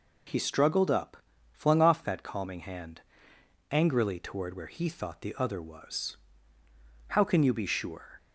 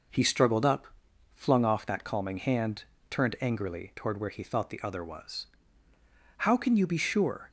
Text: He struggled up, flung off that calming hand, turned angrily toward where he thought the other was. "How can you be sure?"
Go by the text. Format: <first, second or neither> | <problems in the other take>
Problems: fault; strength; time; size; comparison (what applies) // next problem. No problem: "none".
second | skips "turned"; at 3.3 s